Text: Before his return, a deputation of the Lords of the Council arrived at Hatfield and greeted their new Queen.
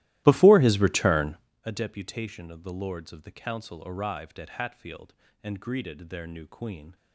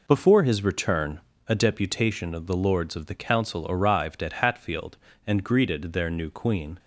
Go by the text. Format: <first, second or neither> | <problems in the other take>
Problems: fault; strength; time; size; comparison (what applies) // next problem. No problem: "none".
second | starts louder than the rest; strong; until 1.5 s; 16 dB